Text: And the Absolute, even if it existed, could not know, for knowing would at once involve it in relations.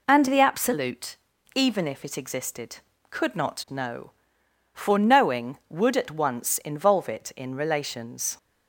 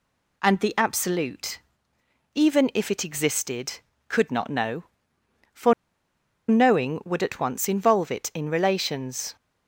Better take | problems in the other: first | pauses between "for" and "knowing"; noticeable; at 5.7 s; 0.76 s long

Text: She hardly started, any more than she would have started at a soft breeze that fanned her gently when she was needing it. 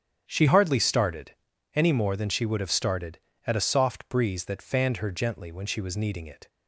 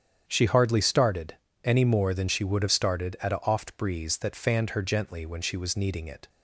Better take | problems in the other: first | starts louder than the rest; strong; until 1.2 s; 8.5 dB; strong in the first // says "oft" for "soft"; at 3.4 s

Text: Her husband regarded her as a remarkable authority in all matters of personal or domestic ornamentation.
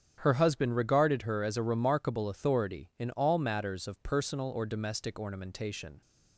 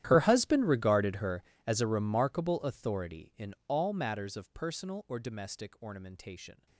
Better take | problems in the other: first | gets quieter; strong; throughout; 23 dB // starts louder than the rest; strong; until 1.0 s; 12 dB; strong in the first

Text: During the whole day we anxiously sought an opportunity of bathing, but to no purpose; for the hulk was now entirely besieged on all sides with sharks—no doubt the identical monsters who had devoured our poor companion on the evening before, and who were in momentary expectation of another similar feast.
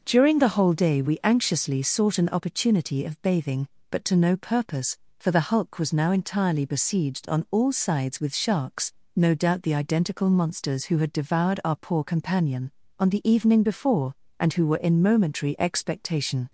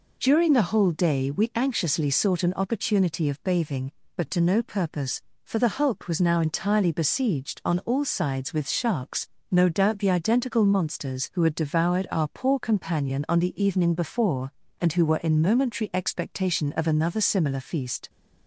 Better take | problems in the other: second | stops before "of another similar feast"; at 16.4 s

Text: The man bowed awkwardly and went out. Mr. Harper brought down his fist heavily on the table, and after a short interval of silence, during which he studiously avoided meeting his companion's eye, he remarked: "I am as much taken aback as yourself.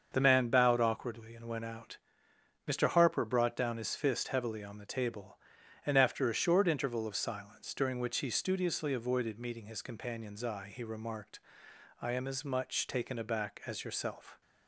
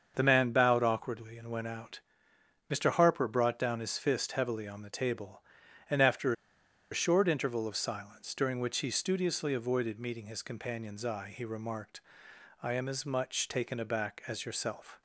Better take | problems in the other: first | starts louder than the rest; until 1.1 s; 6.5 dB; also in the first // pauses between "after" and "a"; noticeable; at 6.3 s; 0.58 s long

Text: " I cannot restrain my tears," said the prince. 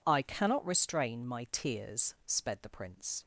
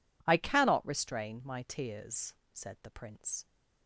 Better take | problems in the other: second | says "sped" for "said"; at 2.2 s

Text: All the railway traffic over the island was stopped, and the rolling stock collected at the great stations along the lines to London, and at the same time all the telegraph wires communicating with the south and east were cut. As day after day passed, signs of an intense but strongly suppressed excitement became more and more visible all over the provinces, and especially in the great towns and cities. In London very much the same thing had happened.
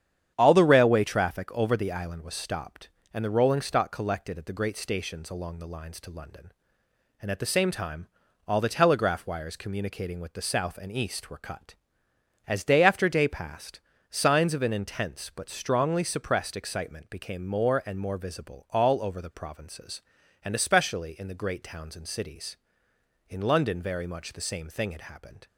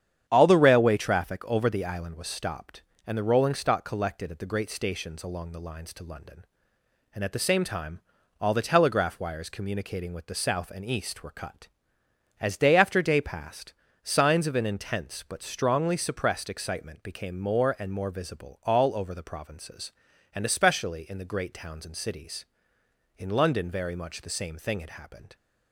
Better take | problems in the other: neither | starts louder than the rest; strong; the same in both // pauses between "time" and "all"; the same in both

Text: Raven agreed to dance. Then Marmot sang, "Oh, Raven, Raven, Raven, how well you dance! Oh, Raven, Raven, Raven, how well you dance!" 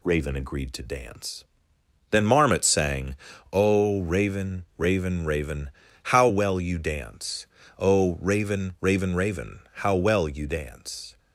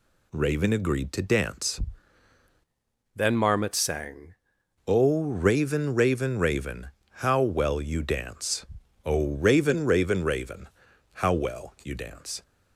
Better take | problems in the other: first | changes voice from "Then" to "sang"; from 3.1 to 4.3 s; 1.2 s long

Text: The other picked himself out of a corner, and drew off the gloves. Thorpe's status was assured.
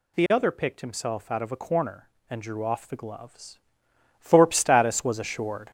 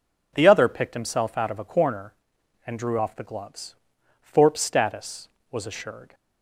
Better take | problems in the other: second | gets louder; noticeable; throughout; 6 dB

